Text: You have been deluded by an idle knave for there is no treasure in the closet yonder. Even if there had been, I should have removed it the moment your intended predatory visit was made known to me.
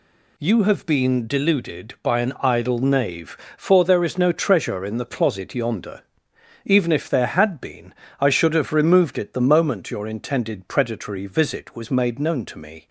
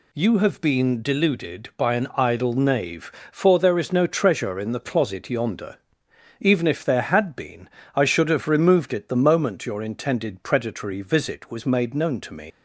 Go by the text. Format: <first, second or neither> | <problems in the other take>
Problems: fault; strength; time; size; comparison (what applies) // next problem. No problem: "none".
first | leaves "me" unfinished; at 12.5 s; 130 ms